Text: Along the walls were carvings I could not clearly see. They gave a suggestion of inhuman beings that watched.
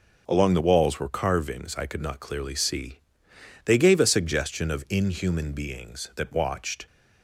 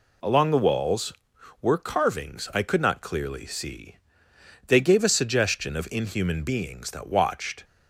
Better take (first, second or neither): neither